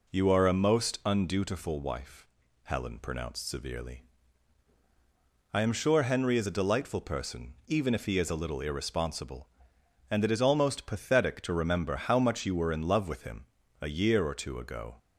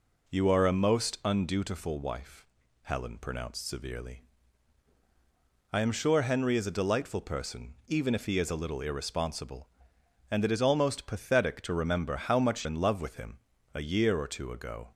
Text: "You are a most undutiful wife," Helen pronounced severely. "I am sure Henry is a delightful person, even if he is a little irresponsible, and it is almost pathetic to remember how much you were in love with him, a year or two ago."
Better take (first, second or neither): first